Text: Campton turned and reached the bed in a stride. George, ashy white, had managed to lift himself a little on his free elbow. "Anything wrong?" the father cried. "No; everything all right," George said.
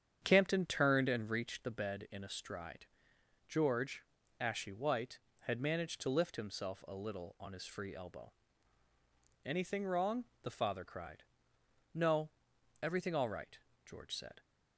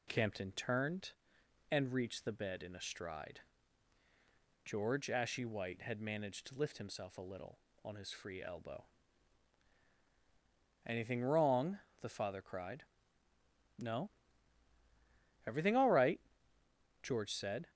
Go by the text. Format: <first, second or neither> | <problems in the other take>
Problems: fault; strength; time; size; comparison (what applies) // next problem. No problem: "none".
second | starts louder than the rest; strong; until 1.5 s; 8.5 dB